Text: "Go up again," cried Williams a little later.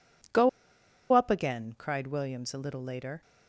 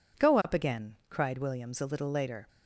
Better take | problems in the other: second | pauses between "Go" and "up"; noticeable; at 0.4 s; 0.63 s long

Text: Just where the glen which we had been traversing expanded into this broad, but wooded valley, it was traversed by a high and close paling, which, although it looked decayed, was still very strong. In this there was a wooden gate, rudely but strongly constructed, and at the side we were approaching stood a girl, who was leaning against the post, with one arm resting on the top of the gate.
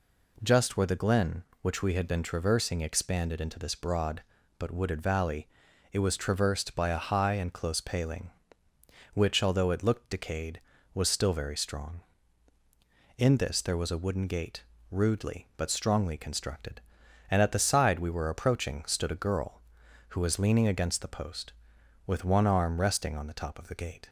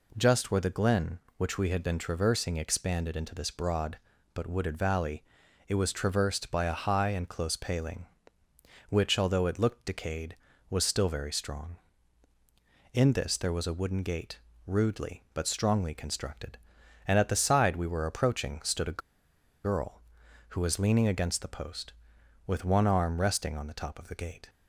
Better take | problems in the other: first | pauses between "a" and "girl"; noticeable; at 19.0 s; 0.64 s long

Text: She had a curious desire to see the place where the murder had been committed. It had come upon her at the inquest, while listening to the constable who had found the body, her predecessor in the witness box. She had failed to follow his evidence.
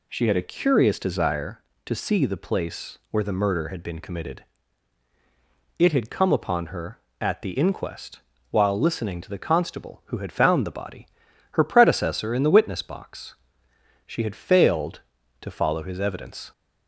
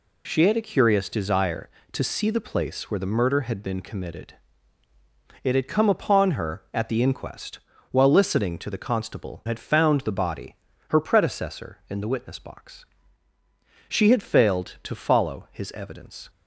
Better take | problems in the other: first | skips "who"; at 9.4 s

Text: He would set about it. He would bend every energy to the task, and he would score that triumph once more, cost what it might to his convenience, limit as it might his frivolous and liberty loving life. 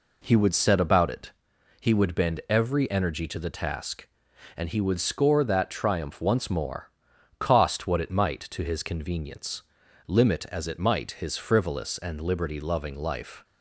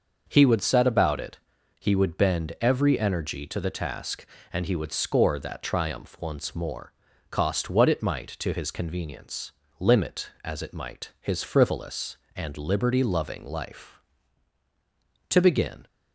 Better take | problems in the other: first | starts louder than the rest; until 1.2 s; 6 dB // goes on to say "To begin"; from 15.2 s on; 0.58 s long

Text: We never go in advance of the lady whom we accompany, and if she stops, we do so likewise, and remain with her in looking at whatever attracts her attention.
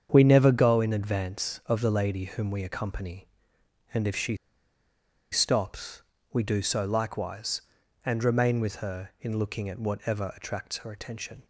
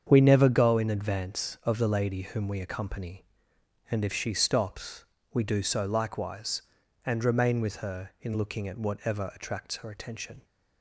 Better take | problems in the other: second | starts louder than the rest; strong; until 1.1 s; 7.5 dB; strong in the second // pauses between "she" and "stops"; noticeable; at 4.3 s; 0.97 s long

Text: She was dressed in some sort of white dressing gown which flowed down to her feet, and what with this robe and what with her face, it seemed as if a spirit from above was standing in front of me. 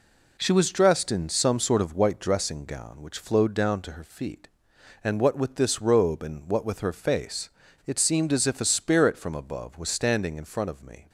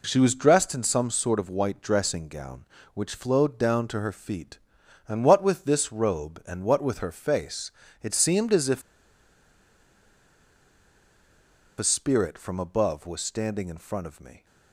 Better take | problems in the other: first | pauses between "if" and "a"; strong; at 8.8 s; 2.9 s long

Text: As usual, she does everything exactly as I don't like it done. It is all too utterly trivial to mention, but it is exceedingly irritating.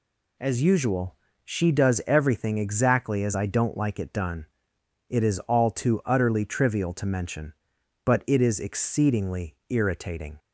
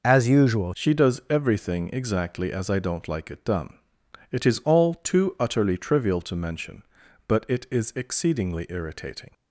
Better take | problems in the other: first | changes voice at "she"; from 0.7 s on; 8.6 s long

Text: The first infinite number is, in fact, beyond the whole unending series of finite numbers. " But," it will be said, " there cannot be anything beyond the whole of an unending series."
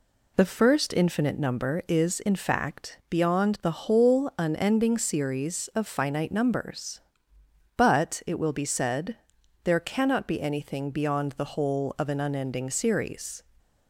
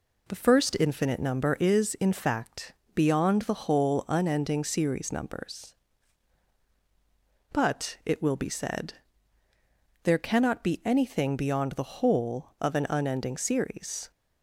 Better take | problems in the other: first | skips "of finite"; at 5.1 s

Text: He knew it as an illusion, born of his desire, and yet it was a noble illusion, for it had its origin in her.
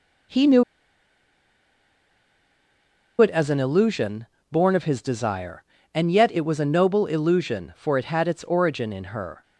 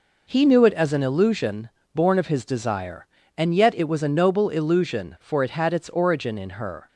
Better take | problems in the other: second | pauses between "knew" and "it"; strong; at 0.6 s; 2.5 s long

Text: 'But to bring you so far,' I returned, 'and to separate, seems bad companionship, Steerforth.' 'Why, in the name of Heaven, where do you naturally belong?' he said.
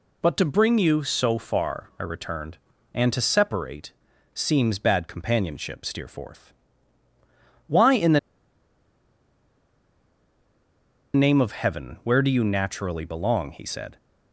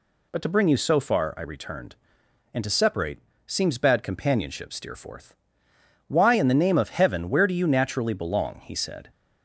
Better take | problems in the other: second | pauses between "the" and "name"; strong; at 8.1 s; 2.9 s long

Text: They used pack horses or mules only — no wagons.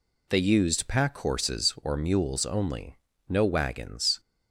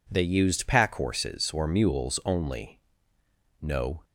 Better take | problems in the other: first | stops before "wagons"; at 4.0 s

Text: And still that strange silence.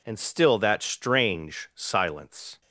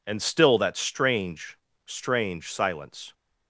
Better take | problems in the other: first | says "strange" twice; at 1.8 s

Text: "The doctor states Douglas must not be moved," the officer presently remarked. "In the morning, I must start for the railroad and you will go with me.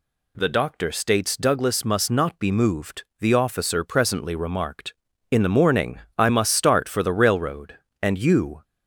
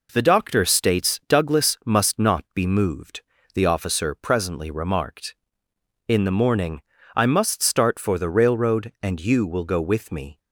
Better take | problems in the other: second | stops before "will go with me"; at 8.6 s

